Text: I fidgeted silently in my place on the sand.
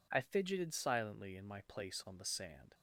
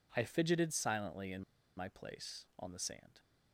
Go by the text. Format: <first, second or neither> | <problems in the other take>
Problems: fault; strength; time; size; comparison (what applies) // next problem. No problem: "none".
first | pauses between "in" and "my"; slight; at 1.4 s; 0.34 s long